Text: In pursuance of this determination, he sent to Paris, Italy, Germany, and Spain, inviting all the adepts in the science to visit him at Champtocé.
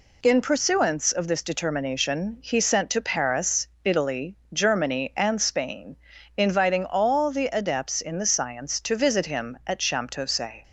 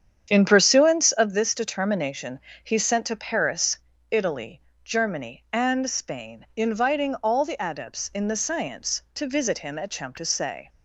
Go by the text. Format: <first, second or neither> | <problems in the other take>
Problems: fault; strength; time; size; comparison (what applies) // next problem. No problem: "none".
first | starts louder than the rest; strong; until 1.3 s; 8.5 dB